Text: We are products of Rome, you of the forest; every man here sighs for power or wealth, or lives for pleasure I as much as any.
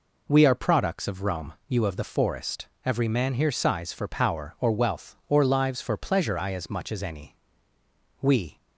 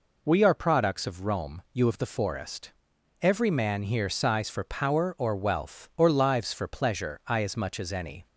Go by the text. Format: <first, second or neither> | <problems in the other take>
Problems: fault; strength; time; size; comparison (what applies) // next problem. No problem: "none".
second | goes on to say "We"; slight; from 8.2 s on; 0.34 s long